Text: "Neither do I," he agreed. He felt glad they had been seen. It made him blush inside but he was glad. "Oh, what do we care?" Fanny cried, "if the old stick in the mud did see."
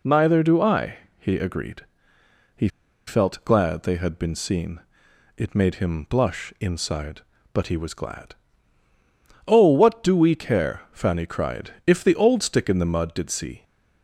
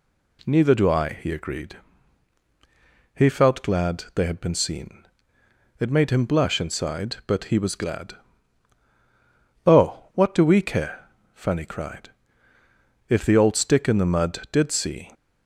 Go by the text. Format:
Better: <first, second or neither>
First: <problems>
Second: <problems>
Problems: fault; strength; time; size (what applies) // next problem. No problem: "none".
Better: second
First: pauses between "He" and "felt"; at 2.6 s; 0.38 s long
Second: none